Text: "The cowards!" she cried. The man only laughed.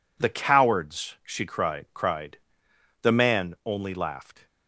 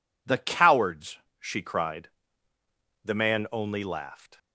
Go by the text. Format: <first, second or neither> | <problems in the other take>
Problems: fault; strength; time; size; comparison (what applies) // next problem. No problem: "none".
second | says "cried" twice; at 1.9 s